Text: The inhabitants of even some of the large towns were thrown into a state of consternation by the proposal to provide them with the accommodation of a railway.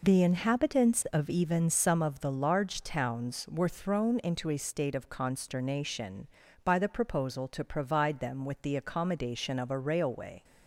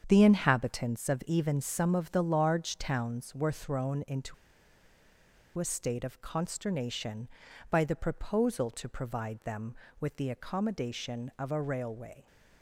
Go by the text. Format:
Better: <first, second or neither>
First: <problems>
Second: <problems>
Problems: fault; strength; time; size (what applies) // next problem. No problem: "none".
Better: first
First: none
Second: starts louder than the rest; strong; until 1.0 s; 7.5 dB // pauses between "into" and "a"; at 4.3 s; 1.2 s long